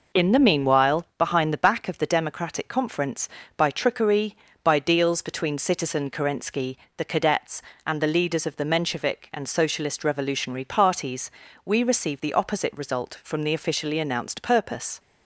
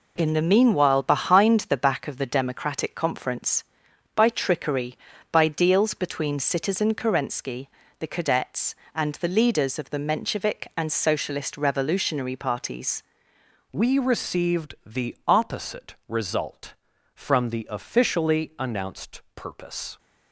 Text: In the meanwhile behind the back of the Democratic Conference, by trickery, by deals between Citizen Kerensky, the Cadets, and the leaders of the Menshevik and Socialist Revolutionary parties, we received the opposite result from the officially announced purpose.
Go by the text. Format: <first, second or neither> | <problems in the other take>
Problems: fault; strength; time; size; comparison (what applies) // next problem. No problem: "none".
first | changes voice at "we"; from 13.7 s on; 6.2 s long